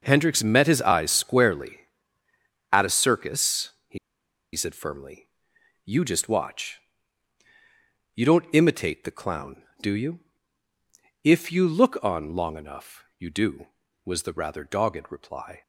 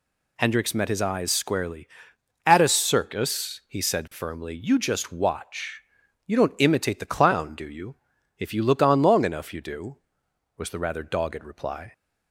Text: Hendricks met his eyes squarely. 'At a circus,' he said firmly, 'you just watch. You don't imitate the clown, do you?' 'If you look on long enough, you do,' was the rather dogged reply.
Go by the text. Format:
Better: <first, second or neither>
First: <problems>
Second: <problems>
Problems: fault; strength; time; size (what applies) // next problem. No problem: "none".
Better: second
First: pauses between "he" and "said"; noticeable; at 3.9 s; 0.57 s long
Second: none